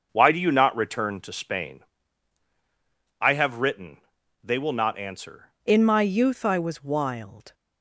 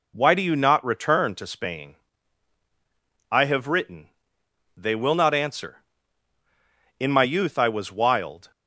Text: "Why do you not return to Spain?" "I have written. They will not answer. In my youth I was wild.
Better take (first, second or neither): second